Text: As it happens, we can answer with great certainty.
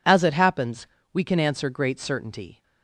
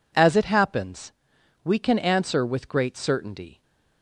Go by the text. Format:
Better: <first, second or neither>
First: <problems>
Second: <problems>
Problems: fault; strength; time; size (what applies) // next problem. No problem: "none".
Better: second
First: skips "with"; at 1.7 s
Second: none